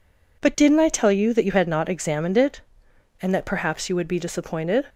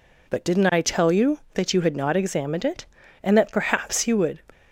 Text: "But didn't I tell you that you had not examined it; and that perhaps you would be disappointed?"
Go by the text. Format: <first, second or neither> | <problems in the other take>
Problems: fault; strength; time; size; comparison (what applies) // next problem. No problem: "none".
first | stops before "be disappointed"; at 4.5 s